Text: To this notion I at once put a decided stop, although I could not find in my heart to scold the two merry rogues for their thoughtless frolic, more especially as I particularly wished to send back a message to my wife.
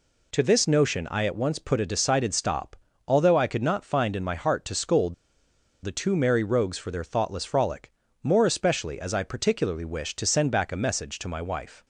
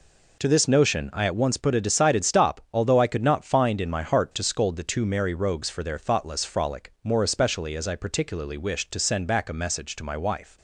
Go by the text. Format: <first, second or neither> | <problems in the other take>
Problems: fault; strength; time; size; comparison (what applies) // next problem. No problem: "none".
second | pauses between "scold" and "the"; noticeable; at 5.1 s; 0.68 s long